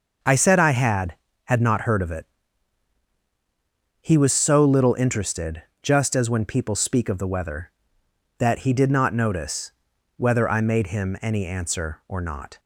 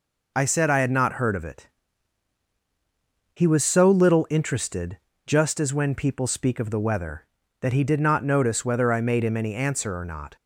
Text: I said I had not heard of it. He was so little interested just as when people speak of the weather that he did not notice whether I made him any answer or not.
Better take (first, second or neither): second